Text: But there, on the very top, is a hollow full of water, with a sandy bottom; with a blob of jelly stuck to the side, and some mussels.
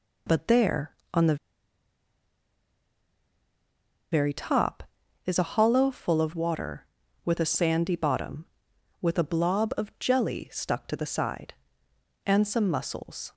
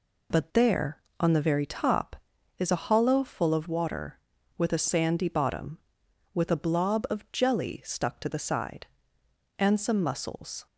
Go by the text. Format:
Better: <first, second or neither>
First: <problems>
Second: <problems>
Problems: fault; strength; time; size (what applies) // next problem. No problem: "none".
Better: second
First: pauses between "the" and "very"; strong; at 1.3 s; 2.7 s long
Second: none